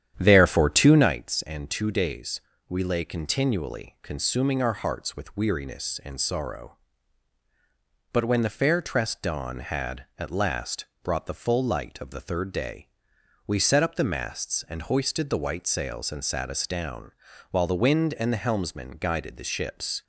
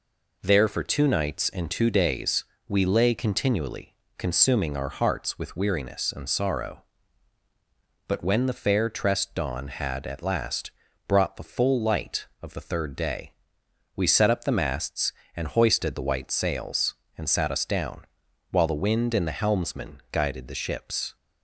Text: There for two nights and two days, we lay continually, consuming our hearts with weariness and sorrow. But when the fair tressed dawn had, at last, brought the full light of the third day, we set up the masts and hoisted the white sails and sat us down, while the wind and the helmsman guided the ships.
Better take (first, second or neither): second